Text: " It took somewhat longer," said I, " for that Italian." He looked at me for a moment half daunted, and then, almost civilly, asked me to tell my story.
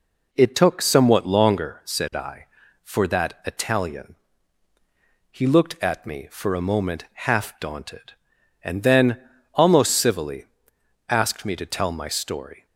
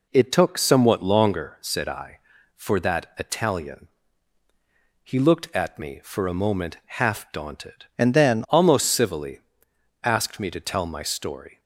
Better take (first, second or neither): first